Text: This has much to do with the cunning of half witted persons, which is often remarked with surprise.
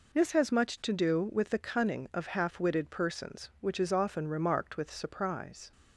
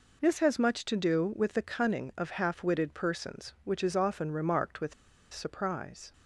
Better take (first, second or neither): first